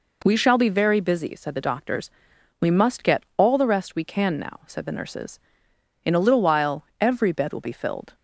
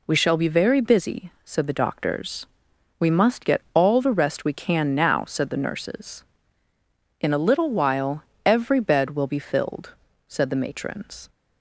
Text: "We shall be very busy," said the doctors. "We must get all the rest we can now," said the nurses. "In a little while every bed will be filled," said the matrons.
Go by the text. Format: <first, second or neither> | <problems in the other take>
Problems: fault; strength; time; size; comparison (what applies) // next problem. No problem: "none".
second | pauses between "while" and "every"; slight; at 6.8 s; 0.16 s long; slight in the second // stops before "said the matrons"; at 8.1 s